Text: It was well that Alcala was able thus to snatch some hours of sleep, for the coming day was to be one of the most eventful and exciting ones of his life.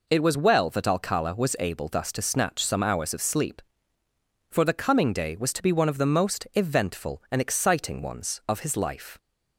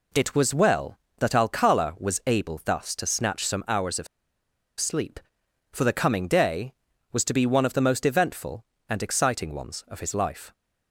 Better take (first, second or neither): first